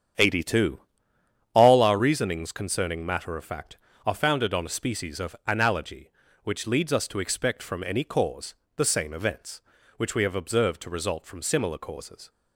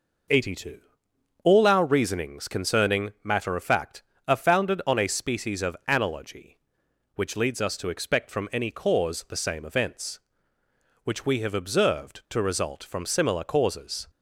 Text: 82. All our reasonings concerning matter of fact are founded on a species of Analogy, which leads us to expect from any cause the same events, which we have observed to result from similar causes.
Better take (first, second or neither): second